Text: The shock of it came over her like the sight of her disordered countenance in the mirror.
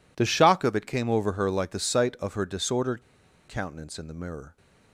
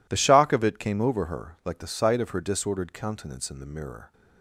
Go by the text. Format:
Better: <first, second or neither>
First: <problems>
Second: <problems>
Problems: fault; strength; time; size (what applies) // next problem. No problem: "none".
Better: second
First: pauses between "disordered" and "countenance"; noticeable; at 3.0 s; 0.47 s long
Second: none